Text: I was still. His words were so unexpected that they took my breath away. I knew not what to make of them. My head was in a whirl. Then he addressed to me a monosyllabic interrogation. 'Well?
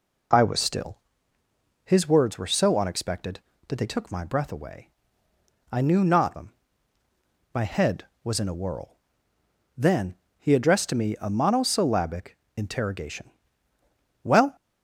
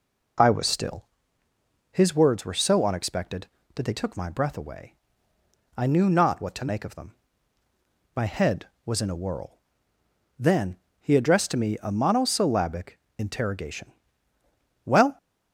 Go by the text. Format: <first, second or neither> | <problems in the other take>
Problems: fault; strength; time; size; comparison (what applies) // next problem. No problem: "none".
second | skips "what to make of"; at 6.3 s // pauses between "Then" and "he"; slight; at 10.1 s; 0.24 s long; slight in the second // pauses between "monosyllabic" and "interrogation"; slight; at 12.3 s; 0.18 s long; slight in the second